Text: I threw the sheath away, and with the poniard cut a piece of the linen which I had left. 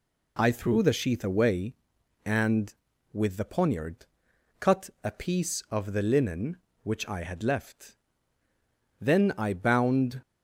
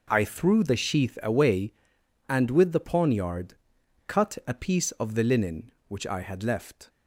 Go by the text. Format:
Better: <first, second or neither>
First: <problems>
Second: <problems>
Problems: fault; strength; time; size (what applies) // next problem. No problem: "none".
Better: second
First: pauses between "poniard" and "cut"; noticeable; at 4.0 s; 0.54 s long // goes on to say "Then I bound"; noticeable; from 9.0 s on; 1.2 s long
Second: pauses between "poniard" and "cut"; noticeable; at 3.5 s; 0.52 s long